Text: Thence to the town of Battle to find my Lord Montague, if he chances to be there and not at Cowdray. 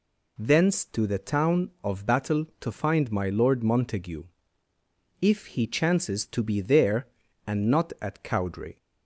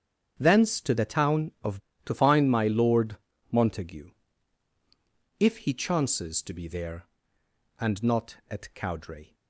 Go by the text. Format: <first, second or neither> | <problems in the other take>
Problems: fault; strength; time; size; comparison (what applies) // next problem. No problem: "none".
first | starts louder than the rest; strong; until 1.3 s; 8 dB // skips "Battle"; at 1.9 s // pauses between "Lord" and "Montague"; slight; at 3.1 s; 0.34 s long